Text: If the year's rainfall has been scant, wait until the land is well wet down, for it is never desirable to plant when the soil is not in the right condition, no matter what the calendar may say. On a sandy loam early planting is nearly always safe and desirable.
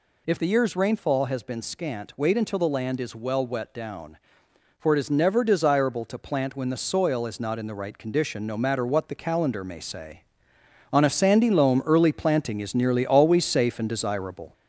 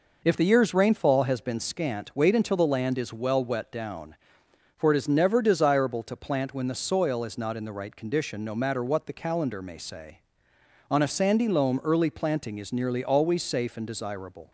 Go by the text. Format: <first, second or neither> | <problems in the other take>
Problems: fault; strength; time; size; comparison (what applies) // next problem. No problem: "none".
second | gets louder; throughout; 4 dB